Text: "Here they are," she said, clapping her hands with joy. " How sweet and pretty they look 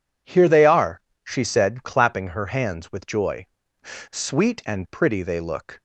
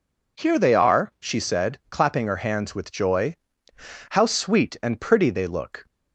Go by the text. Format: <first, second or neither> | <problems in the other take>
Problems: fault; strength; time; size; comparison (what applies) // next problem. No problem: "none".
second | skips "How"; at 4.1 s